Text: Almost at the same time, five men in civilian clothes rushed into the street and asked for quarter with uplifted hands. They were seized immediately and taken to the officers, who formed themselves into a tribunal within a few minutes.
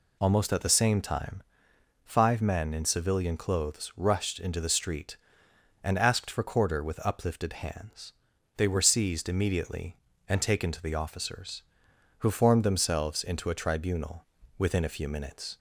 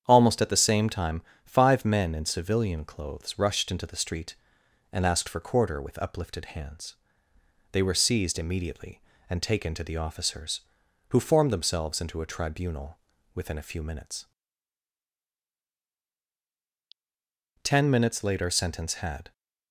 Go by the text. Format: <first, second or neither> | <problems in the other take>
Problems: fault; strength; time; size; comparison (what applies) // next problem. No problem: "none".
first | starts louder than the rest; strong; until 1.0 s; 8.5 dB // pauses between "tribunal" and "within"; at 12.9 s; 0.38 s long; slight in the first // goes on to say "Ten minutes later sentence had"; strong; from 17.6 s on; 1.7 s long